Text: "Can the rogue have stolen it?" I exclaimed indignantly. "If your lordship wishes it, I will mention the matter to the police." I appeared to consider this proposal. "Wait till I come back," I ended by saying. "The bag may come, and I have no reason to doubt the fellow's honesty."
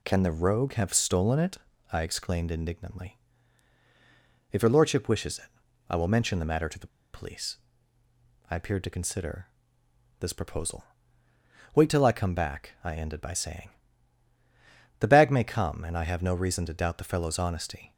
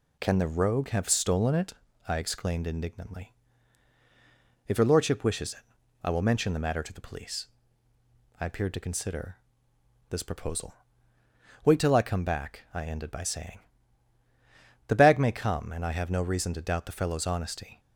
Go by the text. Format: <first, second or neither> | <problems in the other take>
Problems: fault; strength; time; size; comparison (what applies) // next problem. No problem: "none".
second | pauses between "the" and "police"; slight; at 6.8 s; 0.25 s long // pauses between "consider" and "this"; noticeable; at 9.4 s; 0.72 s long; noticeable in the second